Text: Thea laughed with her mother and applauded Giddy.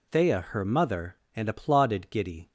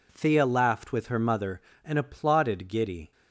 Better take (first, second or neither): second